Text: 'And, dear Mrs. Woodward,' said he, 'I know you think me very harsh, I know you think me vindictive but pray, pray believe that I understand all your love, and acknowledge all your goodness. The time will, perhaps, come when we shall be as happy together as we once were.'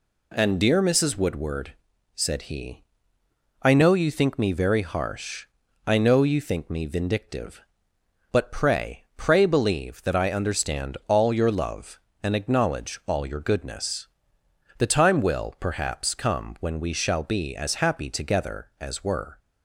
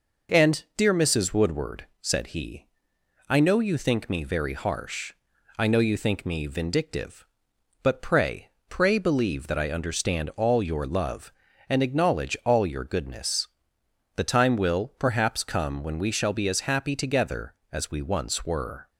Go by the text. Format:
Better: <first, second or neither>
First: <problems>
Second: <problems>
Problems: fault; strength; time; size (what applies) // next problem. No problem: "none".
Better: second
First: skips "we once"; at 19.0 s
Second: none